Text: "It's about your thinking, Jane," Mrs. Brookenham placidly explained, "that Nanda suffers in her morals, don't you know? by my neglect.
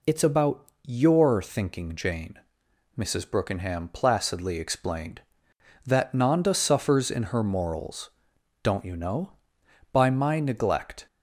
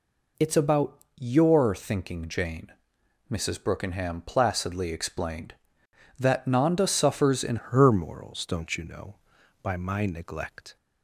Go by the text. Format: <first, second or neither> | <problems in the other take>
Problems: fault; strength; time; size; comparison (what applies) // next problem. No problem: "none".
first | pauses between "about" and "your"; slight; at 0.9 s; 0.18 s long; slight in the first // changes voice at "her"; from 7.5 s on; 3.2 s long